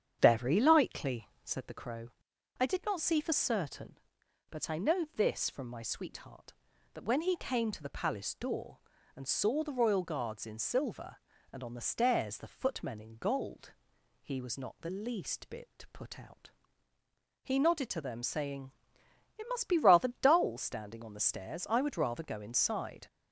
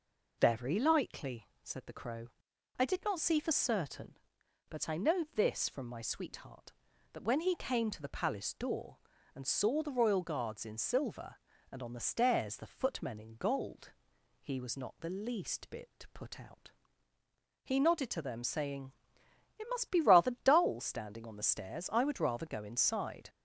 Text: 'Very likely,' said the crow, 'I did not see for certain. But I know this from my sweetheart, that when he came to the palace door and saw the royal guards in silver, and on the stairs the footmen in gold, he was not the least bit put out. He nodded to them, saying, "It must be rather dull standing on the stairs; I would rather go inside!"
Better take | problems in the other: second | starts louder than the rest; strong; until 1.8 s; 8.5 dB

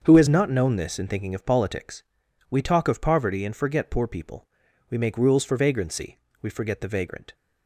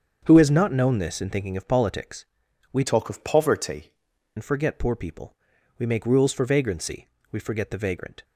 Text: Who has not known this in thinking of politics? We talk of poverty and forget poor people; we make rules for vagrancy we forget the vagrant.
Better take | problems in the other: first | starts louder than the rest; until 1.2 s; 7 dB; also in the first // changes voice from "talk" to "poverty"; from 2.8 to 3.9 s; 1.1 s long // pauses between "vagrancy" and "we"; slight; at 7.0 s; 0.22 s long; slight in the first

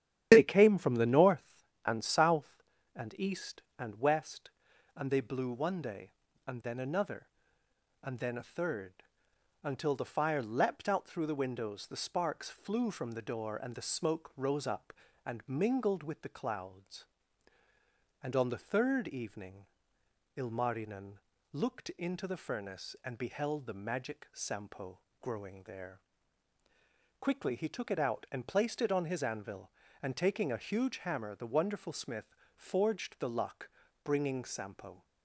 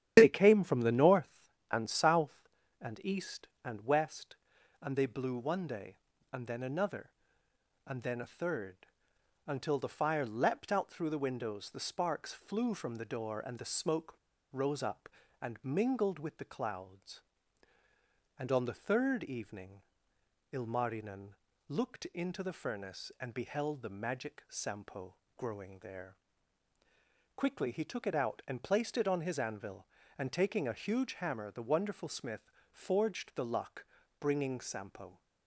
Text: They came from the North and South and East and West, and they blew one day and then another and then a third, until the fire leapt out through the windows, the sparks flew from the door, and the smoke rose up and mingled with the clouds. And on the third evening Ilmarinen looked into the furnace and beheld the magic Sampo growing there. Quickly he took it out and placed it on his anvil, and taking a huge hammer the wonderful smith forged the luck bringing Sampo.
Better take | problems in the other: first | starts louder than the rest; strong; until 1.1 s; 10.5 dB; strong in the first // pauses between "smoke" and "rose"; at 14.1 s; 0.40 s long // pauses between "evening" and "Ilmarinen"; noticeable; at 19.8 s; 0.70 s long; noticeable in the first // pauses between "Ilmarinen" and "looked"; at 21.2 s; 0.40 s long; also in the first // pauses between "Sampo" and "growing"; slight; at 25.1 s; 0.22 s long; slight in the first // pauses between "smith" and "forged"; slight; at 32.5 s; 0.20 s long; slight in the first // pauses between "luck" and "bringing"; slight; at 33.8 s; 0.34 s long; slight in the first

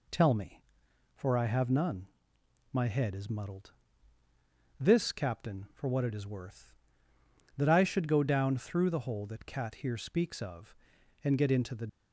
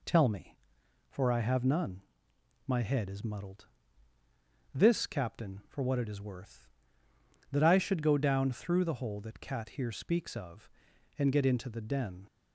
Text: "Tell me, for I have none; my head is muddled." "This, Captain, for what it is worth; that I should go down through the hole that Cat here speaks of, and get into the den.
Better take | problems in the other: second | stops before "den"; at 11.8 s

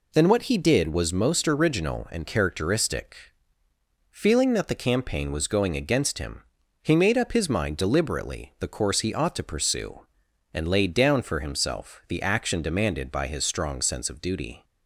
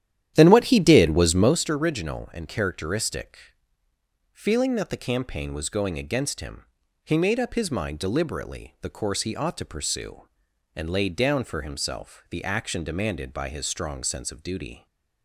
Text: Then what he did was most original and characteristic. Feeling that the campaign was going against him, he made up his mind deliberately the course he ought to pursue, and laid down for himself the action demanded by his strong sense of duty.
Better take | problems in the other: first | starts louder than the rest; strong; until 1.6 s; 11 dB

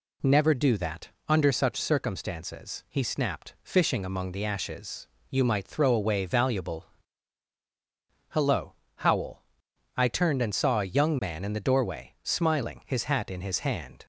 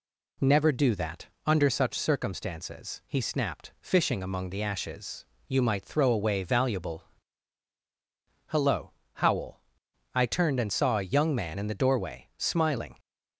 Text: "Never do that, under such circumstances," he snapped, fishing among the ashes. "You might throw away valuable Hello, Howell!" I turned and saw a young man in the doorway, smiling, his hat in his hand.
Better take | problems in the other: first | pauses between "valuable" and "Hello"; strong; at 7.0 s; 1.4 s long; strong in the first // stops before "his hat in his hand"; at 12.9 s

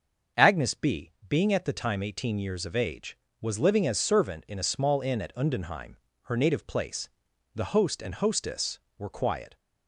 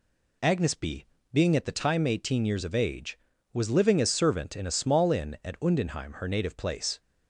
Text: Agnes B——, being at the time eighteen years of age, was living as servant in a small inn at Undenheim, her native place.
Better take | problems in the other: second | starts louder than the rest; until 1.5 s; 6.5 dB // goes on to say "The host and hostess were quiet"; strong; from 7.5 s on; 2.0 s long

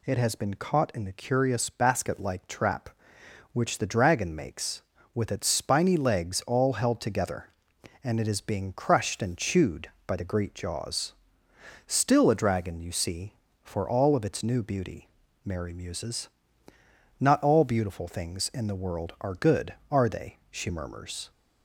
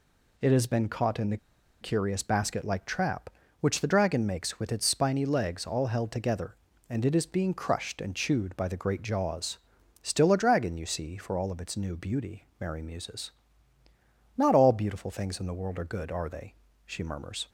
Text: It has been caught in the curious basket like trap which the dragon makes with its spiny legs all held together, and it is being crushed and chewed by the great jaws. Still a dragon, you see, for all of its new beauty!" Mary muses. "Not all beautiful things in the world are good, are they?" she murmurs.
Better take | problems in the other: first | pauses between "the" and "curious"; at 1.3 s; 0.44 s long

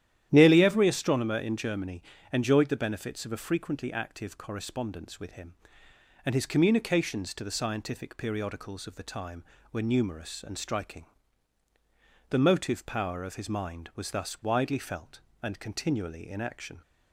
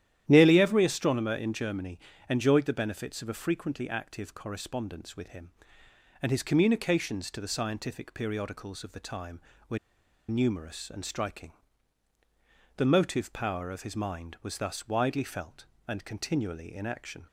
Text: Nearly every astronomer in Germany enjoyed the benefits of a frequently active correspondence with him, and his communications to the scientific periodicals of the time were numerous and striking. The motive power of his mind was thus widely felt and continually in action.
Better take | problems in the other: first | starts louder than the rest; strong; until 1.2 s; 11.5 dB; strong in the first // pauses between "Germany" and "enjoyed"; slight; at 2.0 s; 0.28 s long; slight in the first // pauses between "were" and "numerous"; noticeable; at 9.7 s; 0.50 s long

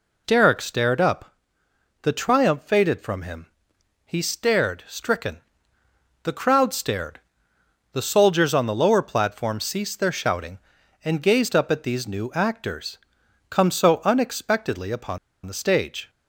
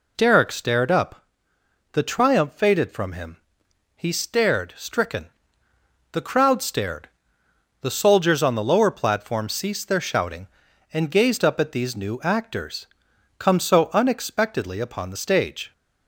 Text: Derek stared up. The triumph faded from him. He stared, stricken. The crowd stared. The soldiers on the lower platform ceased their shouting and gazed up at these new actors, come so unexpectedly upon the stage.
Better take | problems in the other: second | pauses between "upon" and "the"; slight; at 15.1 s; 0.27 s long

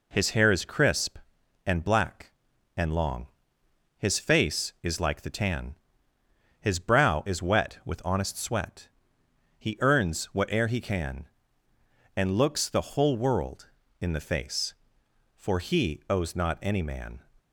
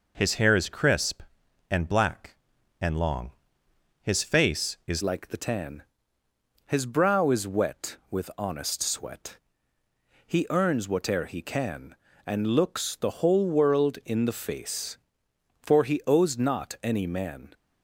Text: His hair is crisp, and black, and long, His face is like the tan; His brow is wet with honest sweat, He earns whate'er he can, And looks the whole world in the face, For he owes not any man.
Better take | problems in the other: first | changes voice at "like"; from 5.0 s on; 12.5 s long

